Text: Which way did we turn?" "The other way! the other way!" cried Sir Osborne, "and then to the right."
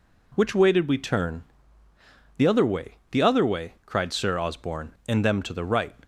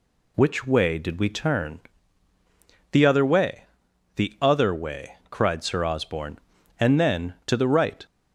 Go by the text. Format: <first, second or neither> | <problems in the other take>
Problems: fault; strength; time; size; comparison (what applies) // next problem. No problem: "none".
second | says "them" for "then"; at 5.2 s